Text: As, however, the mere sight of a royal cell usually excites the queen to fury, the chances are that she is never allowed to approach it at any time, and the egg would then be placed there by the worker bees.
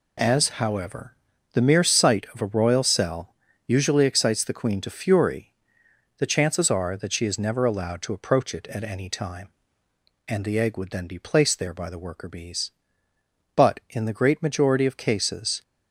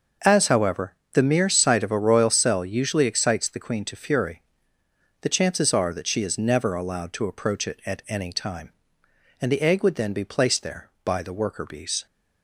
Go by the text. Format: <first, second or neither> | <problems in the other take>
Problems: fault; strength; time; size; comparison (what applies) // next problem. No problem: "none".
second | pauses between "cell" and "usually"; slight; at 3.3 s; 0.32 s long // goes on to say "But in the great majority of cases"; strong; from 13.5 s on; 2.0 s long